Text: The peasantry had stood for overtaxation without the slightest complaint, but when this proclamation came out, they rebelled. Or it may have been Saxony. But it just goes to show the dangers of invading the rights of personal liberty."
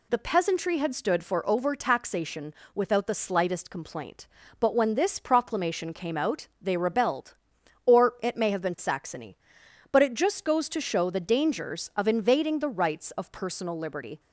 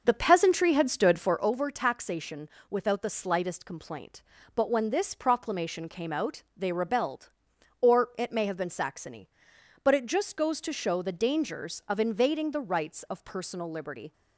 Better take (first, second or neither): first